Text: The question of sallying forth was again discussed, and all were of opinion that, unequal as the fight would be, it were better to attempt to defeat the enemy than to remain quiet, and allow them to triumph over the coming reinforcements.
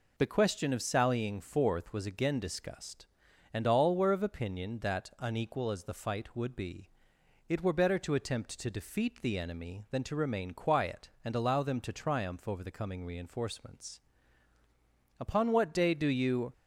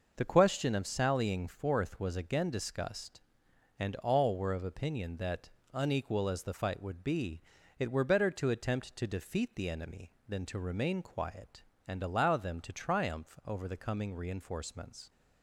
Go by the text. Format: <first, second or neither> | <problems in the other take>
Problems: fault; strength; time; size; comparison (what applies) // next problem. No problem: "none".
second | goes on to say "Upon what day do you"; from 15.1 s on; 1.3 s long